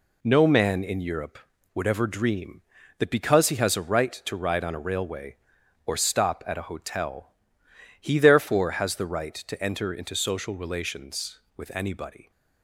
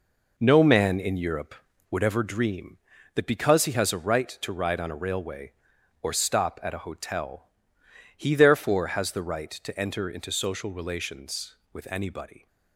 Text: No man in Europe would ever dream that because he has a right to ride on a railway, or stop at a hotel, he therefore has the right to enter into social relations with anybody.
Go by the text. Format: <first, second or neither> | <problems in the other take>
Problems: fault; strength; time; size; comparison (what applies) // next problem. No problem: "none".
first | starts louder than the rest; noticeable; until 2.3 s; 4.5 dB